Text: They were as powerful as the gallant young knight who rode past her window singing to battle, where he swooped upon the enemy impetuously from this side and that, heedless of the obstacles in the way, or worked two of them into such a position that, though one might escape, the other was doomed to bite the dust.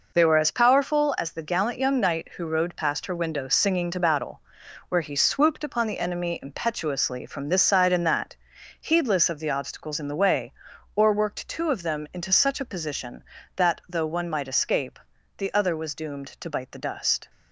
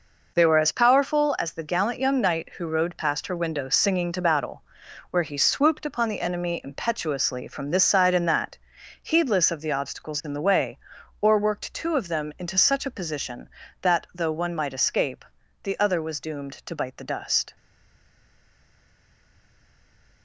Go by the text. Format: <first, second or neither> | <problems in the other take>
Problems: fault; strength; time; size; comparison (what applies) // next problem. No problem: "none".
first | stays silent after the last word; strong; from 17.5 s on; 2.7 s long